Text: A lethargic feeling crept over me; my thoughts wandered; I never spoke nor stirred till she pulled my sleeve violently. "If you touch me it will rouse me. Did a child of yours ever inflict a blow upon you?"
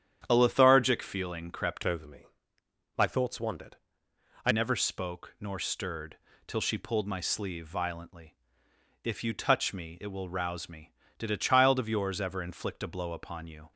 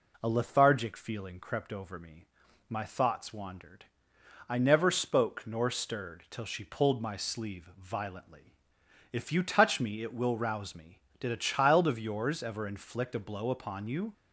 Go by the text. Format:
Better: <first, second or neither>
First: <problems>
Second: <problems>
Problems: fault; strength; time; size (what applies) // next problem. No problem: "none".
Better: second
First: starts louder than the rest; strong; until 1.2 s; 9.5 dB // changes voice from "over" to "I"; from 1.8 to 4.5 s; 2.7 s long // pauses between "stirred" and "till"; slight; at 6.1 s; 0.32 s long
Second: none